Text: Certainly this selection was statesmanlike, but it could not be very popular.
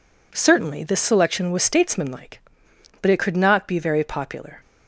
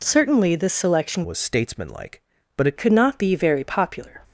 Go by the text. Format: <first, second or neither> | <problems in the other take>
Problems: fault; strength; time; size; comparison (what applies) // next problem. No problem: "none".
first | changes voice from "was" to "it"; from 1.2 to 2.7 s; 1.5 s long